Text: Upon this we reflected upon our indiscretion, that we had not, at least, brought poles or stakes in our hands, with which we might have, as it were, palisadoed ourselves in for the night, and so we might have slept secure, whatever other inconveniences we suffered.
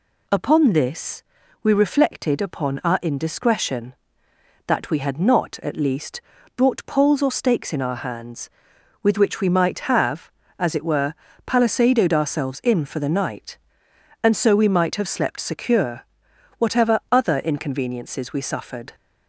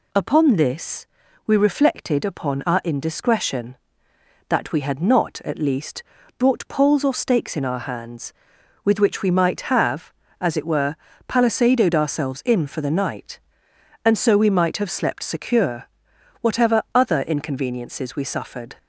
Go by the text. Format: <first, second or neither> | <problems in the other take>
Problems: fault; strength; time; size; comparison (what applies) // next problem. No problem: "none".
neither | pauses between "this" and "we"; the same in both